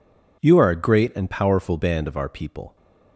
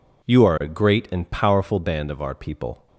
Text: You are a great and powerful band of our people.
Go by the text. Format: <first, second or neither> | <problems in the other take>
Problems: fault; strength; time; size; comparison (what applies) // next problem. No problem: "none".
neither | none